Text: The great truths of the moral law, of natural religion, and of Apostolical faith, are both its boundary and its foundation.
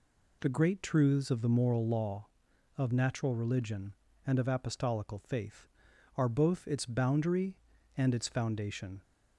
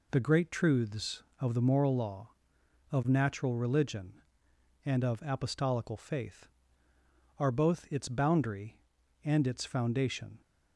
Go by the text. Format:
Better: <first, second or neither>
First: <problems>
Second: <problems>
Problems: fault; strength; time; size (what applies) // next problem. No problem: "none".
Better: neither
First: none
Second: none